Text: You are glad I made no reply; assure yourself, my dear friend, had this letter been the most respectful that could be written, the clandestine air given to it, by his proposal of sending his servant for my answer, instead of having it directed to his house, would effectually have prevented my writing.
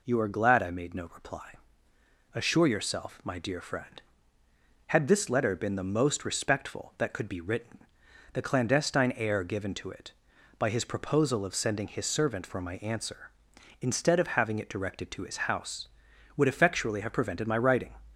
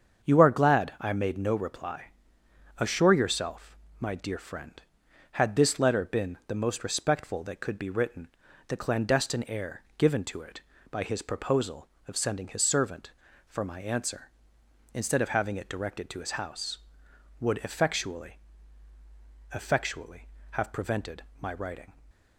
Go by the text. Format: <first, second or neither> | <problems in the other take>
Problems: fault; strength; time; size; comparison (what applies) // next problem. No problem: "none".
first | starts louder than the rest; strong; until 1.3 s; 7 dB // pauses between "air" and "given"; slight; at 9.8 s; 0.16 s long // says "effectually" twice; at 19.5 s // pauses between "prevented" and "my"; slight; at 21.2 s; 0.16 s long